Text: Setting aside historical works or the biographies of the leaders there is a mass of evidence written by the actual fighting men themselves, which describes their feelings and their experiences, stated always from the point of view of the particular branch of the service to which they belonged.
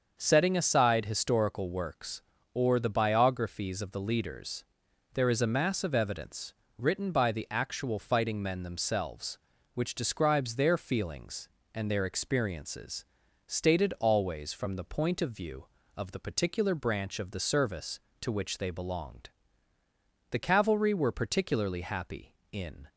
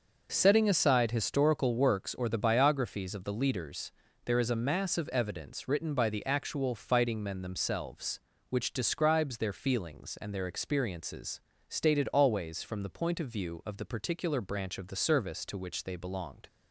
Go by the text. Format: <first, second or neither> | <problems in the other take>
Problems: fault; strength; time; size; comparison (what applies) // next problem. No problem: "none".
second | starts louder than the rest; until 1.1 s; 6.5 dB; noticeable in the second // pauses between "leaders" and "there"; noticeable; at 4.6 s; 0.50 s long; slight in the second // pauses between "evidence" and "written"; slight; at 6.5 s; 0.26 s long // goes on to say "The Cavalry were particularly happy in"; strong; from 20.3 s on; 2.5 s long